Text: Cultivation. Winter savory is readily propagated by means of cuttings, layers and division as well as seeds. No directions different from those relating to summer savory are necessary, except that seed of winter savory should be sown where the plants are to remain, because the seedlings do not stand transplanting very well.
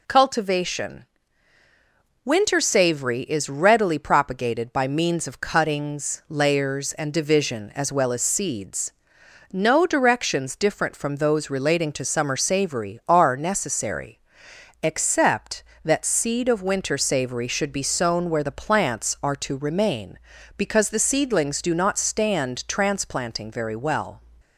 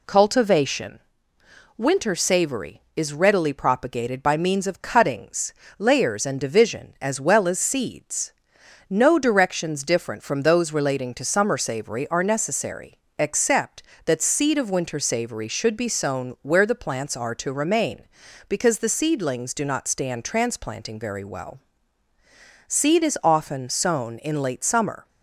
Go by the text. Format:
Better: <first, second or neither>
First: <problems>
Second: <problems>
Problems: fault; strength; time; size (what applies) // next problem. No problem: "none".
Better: first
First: none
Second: goes on to say "Seed is often sown in late summer"; strong; from 22.6 s on; 2.4 s long